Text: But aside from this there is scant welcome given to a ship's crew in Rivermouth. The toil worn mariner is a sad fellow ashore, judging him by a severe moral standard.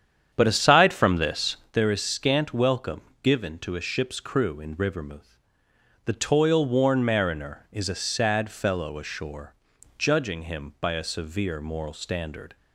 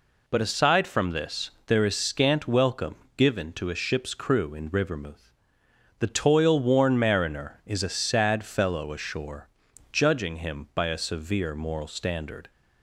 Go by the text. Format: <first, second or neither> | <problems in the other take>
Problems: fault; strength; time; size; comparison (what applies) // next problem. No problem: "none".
second | starts louder than the rest; strong; until 1.7 s; 8.5 dB // pauses between "this" and "there"; slight; at 1.5 s; 0.16 s long; slight in the second // pauses between "welcome" and "given"; slight; at 3.0 s; 0.20 s long; slight in the second